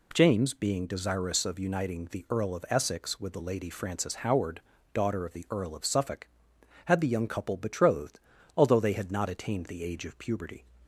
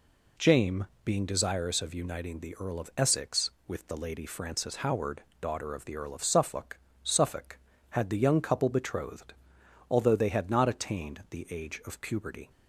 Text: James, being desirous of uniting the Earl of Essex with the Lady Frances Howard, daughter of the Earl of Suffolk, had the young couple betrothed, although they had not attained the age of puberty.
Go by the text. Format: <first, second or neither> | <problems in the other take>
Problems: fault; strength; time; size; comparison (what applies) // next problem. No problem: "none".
first | says "Suffolk" twice; at 7.0 s